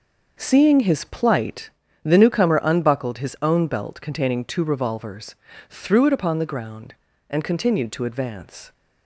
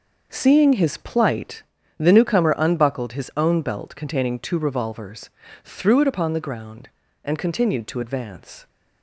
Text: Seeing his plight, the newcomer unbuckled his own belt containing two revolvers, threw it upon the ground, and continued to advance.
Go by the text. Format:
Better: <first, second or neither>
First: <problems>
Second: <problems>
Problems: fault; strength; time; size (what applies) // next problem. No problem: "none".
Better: neither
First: none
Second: none